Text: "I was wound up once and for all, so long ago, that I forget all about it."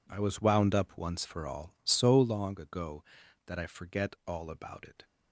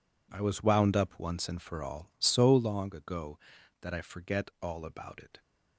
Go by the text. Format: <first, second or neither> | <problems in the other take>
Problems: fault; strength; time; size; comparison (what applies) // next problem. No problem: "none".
second | skips "and"; at 1.2 s